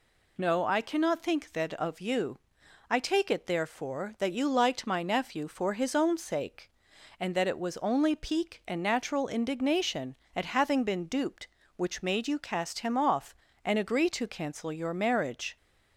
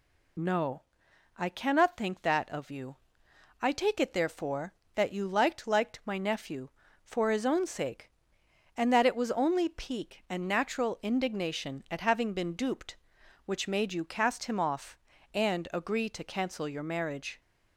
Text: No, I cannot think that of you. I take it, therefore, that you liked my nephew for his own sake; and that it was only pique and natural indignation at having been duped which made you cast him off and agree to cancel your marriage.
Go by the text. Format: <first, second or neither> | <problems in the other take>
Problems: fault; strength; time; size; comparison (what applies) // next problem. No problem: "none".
first | says "liked" twice; at 5.6 s